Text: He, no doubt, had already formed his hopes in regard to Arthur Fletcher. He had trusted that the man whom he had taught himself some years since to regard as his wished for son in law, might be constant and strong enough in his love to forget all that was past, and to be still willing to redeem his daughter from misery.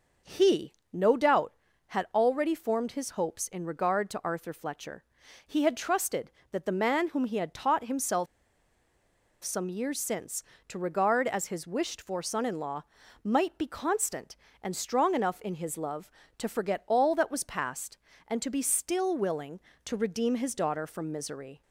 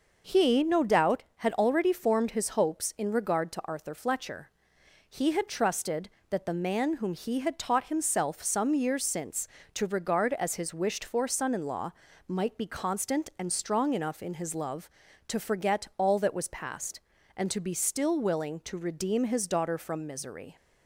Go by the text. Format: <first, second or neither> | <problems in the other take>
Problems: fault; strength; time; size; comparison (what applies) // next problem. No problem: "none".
second | pauses between "himself" and "some"; at 8.2 s; 1.1 s long